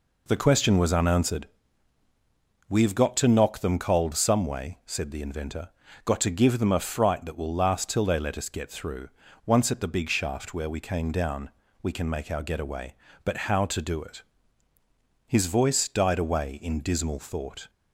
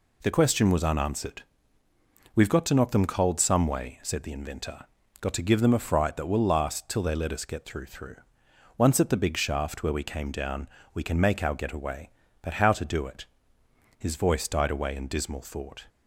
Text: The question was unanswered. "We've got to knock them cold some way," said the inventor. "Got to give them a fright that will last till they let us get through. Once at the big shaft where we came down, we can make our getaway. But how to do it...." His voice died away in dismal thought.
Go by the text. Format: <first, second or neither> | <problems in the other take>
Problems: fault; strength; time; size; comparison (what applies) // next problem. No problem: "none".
first | says "through" twice; at 7.8 s